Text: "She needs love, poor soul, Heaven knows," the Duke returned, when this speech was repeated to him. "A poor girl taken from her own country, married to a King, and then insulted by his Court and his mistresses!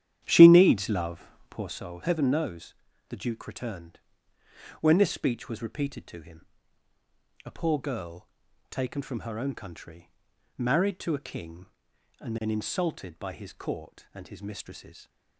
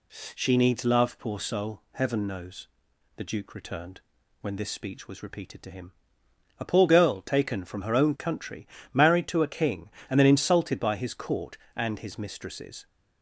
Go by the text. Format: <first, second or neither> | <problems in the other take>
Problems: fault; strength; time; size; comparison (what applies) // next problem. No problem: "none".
second | starts louder than the rest; strong; until 1.8 s; 10.5 dB // pauses between "girl" and "taken"; at 8.2 s; 0.42 s long